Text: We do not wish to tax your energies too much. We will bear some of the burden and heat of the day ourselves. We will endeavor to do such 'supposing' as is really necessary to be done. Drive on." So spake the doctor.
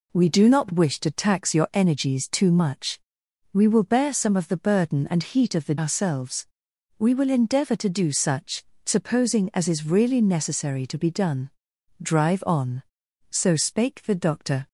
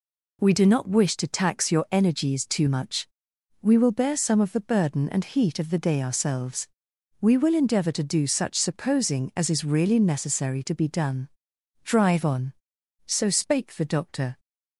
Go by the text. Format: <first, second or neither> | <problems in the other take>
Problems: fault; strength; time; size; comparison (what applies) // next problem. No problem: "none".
second | skips "day"; at 5.7 s // pauses between "such" and "supposing"; slight; at 8.6 s; 0.22 s long